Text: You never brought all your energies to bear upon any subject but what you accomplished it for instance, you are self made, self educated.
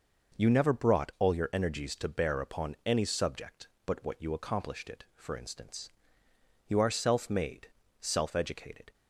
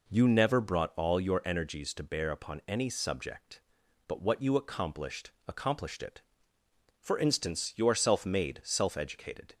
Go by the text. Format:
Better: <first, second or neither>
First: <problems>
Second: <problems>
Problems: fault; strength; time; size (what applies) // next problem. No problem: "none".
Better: first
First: none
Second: says "accomplished" twice; at 5.4 s